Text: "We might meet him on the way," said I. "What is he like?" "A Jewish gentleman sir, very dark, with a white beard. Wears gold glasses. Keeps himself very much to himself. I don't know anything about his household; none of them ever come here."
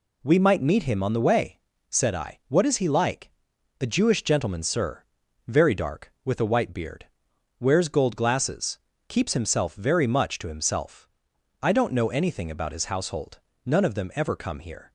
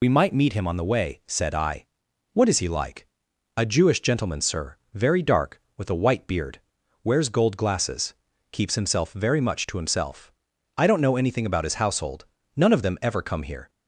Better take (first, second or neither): first